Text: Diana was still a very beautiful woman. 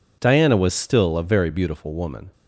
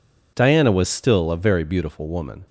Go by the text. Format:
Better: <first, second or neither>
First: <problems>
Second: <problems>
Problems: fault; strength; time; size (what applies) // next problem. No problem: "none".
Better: neither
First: none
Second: none